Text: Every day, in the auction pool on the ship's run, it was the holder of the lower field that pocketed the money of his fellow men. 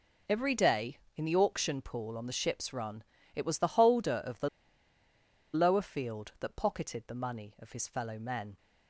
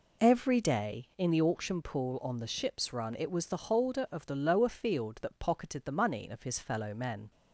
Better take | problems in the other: second | pauses between "the" and "lower"; at 4.4 s; 1.0 s long

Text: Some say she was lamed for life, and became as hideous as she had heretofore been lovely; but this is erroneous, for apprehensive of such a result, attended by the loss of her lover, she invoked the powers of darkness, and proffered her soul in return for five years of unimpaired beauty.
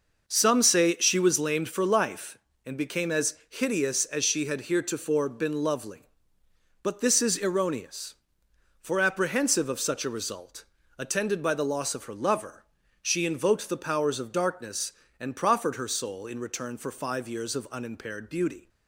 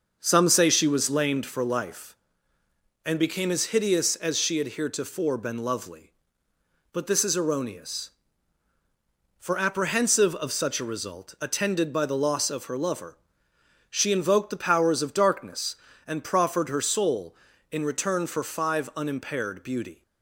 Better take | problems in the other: first | starts louder than the rest; noticeable; until 1.2 s; 6 dB // skips "years of"; at 18.9 s

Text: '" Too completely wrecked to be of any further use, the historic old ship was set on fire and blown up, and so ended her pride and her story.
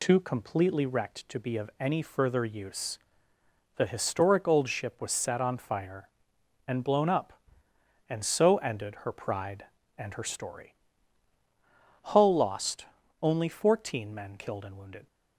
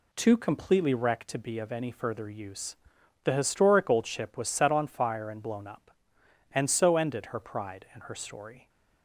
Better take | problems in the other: second | goes on to say "Hull lost only fourteen men killed and wounded"; strong; from 12.0 s on; 3.0 s long

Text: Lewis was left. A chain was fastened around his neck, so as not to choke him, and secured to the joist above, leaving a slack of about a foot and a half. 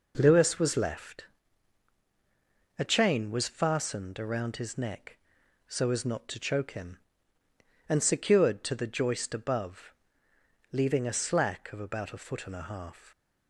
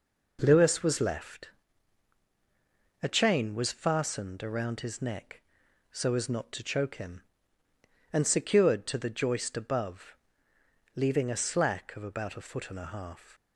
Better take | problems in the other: neither | none

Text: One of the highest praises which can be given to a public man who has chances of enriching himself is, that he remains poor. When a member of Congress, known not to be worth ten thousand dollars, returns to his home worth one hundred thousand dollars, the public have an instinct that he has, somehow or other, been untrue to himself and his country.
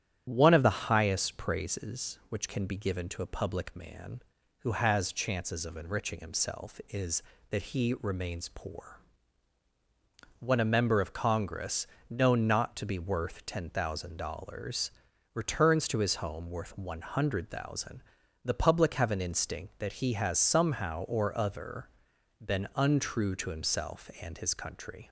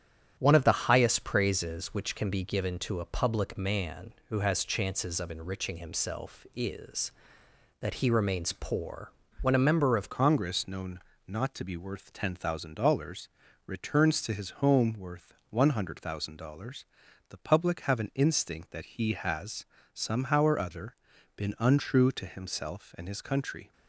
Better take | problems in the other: first | starts louder than the rest; strong; until 1.3 s; 9.5 dB; strong in the first // changes voice at "Congress"; from 10.0 s on; 13.7 s long // pauses between "known" and "not"; slight; at 10.9 s; 0.26 s long // pauses between "worth" and "one"; slight; at 15.3 s; 0.16 s long

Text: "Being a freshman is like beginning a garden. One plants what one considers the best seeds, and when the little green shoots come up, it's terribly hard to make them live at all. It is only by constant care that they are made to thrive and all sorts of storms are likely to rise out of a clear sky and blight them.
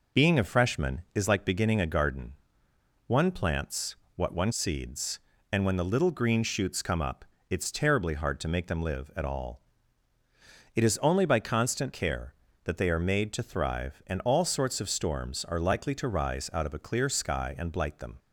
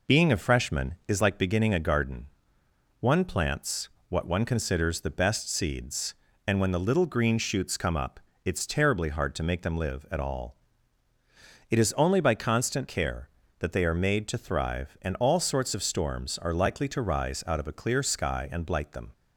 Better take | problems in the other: second | pauses between "plants" and "what"; slight; at 3.9 s; 0.20 s long; slight in the second // skips "considers the best"; at 4.5 s

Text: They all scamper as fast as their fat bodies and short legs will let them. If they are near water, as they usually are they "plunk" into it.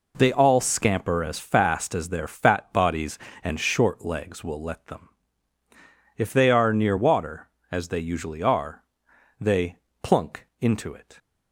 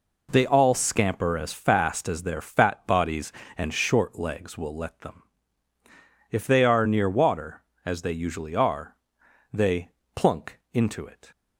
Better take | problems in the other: neither | pauses between "are" and "they"; noticeable; the same in both // pauses between "they" and "plunk"; slight; the same in both

